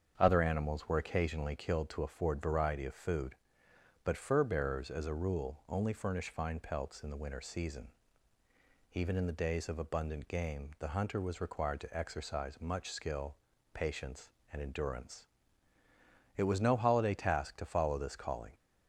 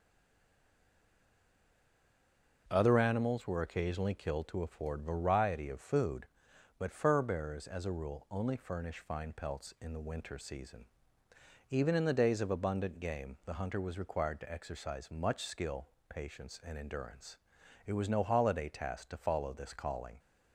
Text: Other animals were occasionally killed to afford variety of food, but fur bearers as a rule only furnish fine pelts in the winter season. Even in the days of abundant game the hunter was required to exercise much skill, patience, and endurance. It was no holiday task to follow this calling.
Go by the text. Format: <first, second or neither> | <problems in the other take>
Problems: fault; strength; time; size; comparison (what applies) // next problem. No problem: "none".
first | stays silent before the first word; strong; until 2.6 s; 2.6 s long // starts louder than the rest; until 3.6 s; 6.5 dB; strong in the first